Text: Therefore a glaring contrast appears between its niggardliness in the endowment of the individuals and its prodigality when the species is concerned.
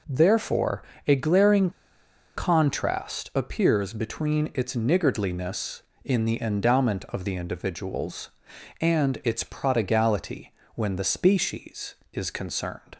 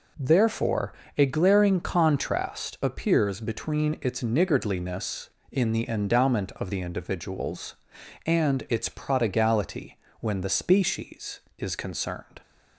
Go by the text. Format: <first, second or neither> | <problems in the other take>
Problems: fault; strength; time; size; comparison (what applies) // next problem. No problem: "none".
second | pauses between "Therefore" and "a"; slight; at 0.8 s; 0.26 s long; slight in the second // pauses between "glaring" and "contrast"; noticeable; at 1.6 s; 0.66 s long // pauses between "prodigality" and "when"; slight; at 10.5 s; 0.24 s long; slight in the second